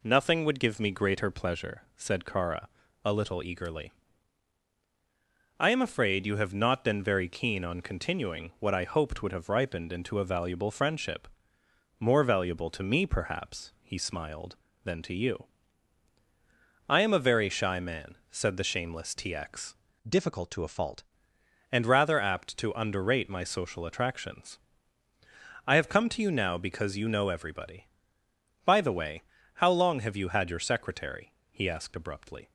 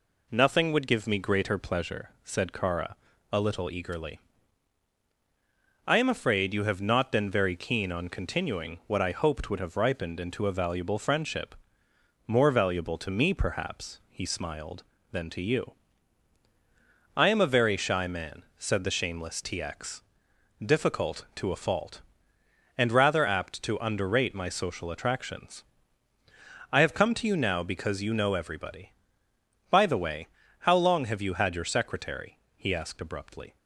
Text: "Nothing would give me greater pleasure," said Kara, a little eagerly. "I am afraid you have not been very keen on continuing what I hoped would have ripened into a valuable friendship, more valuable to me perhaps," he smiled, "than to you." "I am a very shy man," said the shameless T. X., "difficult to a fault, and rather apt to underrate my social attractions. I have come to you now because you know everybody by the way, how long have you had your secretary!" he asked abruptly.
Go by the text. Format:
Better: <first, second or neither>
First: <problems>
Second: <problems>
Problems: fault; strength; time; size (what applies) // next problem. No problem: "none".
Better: second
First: changes voice from "difficult" to "fault"; from 20.0 to 21.0 s; 1.0 s long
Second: none